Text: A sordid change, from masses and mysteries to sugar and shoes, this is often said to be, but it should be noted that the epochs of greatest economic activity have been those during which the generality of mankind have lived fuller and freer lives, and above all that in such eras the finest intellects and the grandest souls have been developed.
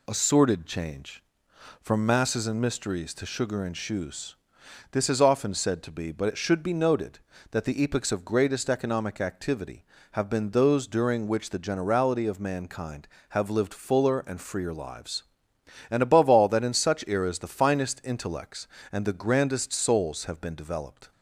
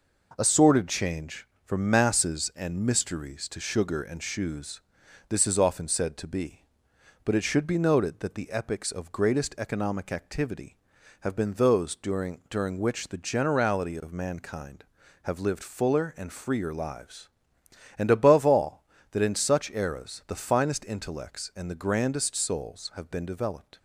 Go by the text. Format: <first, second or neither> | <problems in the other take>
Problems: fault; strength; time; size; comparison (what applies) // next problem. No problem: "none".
first | says "during" twice; at 12.4 s